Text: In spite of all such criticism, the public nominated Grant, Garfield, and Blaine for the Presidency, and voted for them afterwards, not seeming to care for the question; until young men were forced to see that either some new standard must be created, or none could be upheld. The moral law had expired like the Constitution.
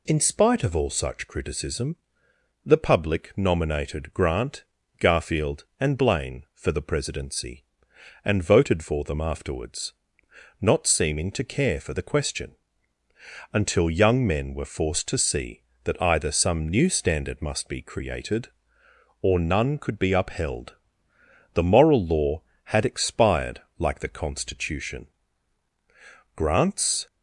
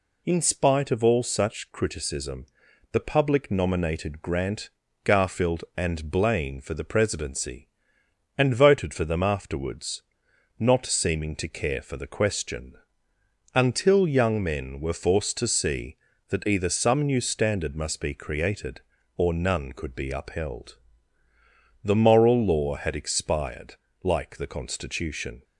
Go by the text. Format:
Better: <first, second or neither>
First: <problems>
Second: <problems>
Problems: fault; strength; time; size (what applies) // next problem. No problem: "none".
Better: second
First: pauses between "expired" and "like"; slight; at 23.6 s; 0.16 s long // goes on to say "Grant's"; noticeable; from 26.3 s on; 0.70 s long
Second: pauses between "expired" and "like"; slight; at 23.7 s; 0.26 s long